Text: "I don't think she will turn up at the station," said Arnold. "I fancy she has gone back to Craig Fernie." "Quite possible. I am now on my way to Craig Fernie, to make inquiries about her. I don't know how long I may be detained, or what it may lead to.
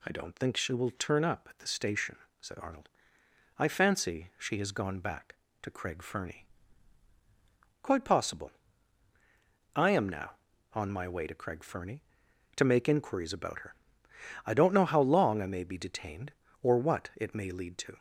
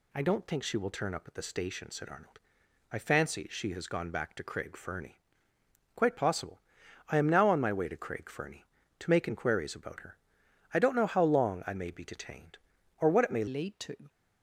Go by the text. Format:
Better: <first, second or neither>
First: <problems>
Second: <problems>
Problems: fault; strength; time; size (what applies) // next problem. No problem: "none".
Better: first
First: none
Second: changes voice at "lead"; from 13.4 s on; 0.6 s long